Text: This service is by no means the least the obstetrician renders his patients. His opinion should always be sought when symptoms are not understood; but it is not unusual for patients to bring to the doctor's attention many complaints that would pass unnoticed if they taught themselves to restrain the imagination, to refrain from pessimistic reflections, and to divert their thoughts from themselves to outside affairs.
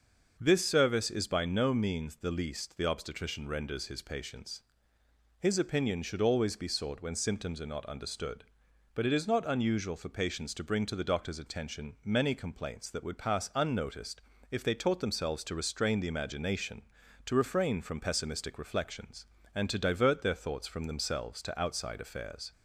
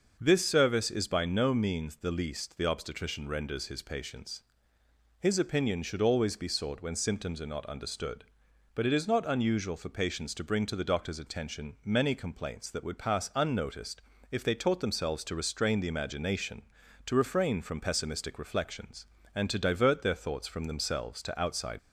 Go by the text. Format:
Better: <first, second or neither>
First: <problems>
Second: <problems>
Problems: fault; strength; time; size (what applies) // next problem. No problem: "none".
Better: first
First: starts louder than the rest; until 1.4 s; 6 dB // pauses between "unnoticed" and "if"; slight; at 14.2 s; 0.30 s long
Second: starts louder than the rest; until 1.2 s; 6 dB // pauses between "unnoticed" and "if"; slight; at 14.0 s; 0.30 s long // stops before "affairs"; at 21.7 s